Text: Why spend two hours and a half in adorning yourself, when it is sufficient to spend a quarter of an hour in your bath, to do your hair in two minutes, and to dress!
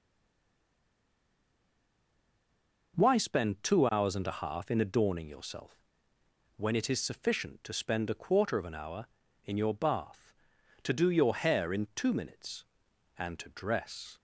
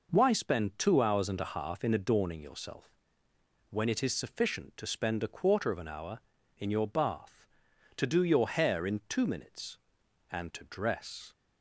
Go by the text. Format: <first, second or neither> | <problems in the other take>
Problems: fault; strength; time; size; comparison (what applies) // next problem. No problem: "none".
second | stays silent before the first word; strong; until 2.9 s; 2.9 s long